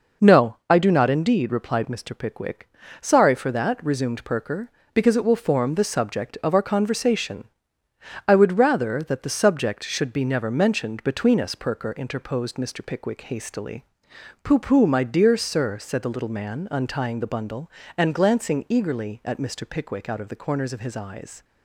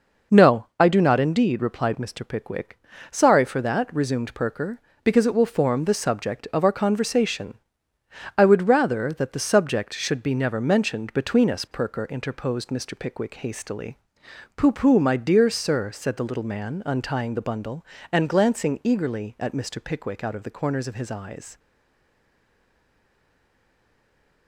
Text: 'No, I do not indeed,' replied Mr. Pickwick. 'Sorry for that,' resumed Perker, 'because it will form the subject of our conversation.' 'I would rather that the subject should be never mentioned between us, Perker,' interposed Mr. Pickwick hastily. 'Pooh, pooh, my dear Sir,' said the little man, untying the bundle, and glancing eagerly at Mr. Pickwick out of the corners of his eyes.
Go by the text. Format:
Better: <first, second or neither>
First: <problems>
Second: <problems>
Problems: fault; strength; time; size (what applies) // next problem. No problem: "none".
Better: first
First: none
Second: stays silent after the last word; strong; from 21.5 s on; 2.9 s long